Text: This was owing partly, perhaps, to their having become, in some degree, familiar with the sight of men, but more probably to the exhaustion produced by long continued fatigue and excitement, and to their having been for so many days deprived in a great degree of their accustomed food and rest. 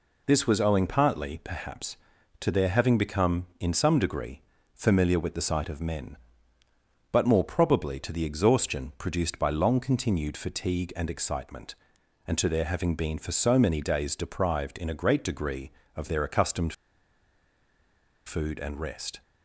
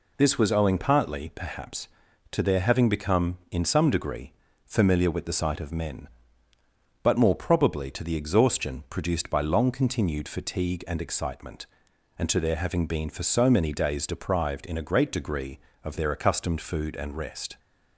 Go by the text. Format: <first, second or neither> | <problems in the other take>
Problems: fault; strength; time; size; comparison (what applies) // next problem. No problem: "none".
second | pauses between "accustomed" and "food"; strong; at 16.7 s; 1.5 s long